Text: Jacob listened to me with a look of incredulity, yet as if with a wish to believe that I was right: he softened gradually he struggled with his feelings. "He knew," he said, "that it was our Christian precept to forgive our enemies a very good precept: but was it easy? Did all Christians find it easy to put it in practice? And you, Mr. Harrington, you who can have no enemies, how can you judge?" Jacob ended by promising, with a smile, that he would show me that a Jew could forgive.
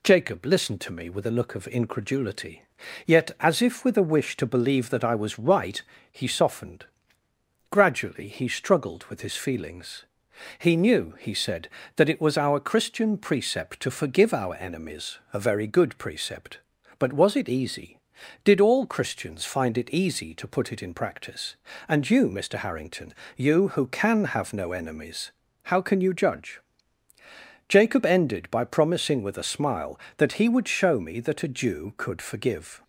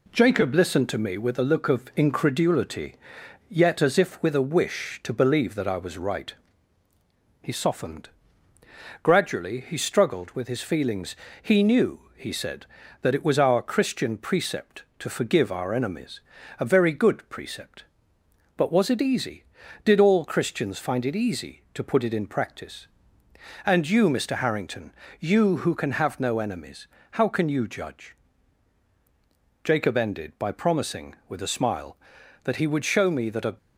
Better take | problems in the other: first | pauses between "softened" and "gradually"; noticeable; at 8.0 s; 0.94 s long; noticeable in the first // pauses between "enemies" and "a"; at 16.2 s; 0.38 s long // stops before "Jew could forgive"; at 33.5 s

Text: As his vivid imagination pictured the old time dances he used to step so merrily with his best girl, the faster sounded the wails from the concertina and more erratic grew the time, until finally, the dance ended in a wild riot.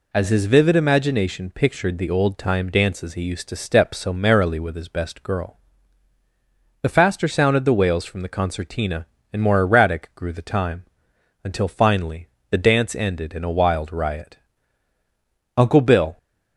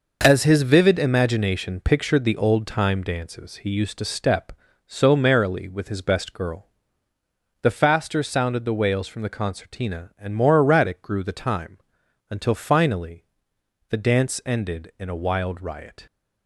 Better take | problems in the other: second | goes on to say "Uncle Bill"; from 15.5 s on; 0.60 s long

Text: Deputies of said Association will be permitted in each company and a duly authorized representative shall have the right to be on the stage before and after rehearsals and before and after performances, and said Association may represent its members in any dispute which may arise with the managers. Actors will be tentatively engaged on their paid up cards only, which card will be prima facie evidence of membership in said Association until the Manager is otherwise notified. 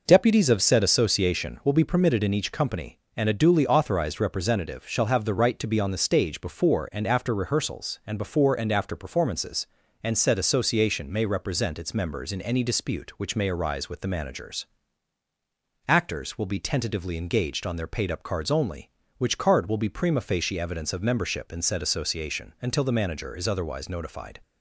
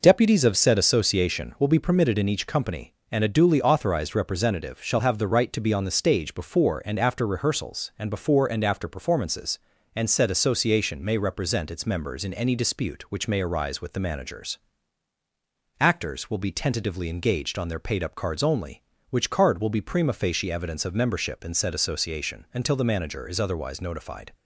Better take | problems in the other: neither | none

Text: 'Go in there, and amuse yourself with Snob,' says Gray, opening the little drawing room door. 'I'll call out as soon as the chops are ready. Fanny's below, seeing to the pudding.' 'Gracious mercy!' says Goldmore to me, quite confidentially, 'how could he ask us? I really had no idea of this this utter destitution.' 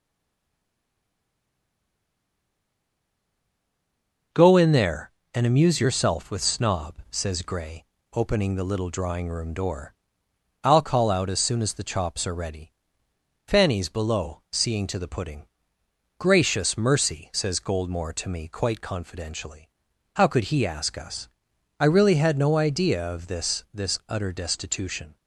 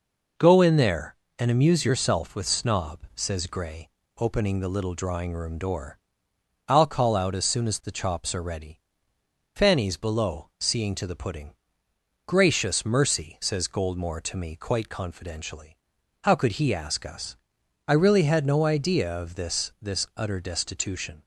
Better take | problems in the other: second | stays silent before the first word; strong; until 4.3 s; 4.3 s long

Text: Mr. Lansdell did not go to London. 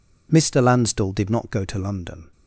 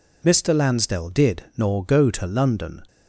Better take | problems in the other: first | says "nor" for "not"; at 1.5 s

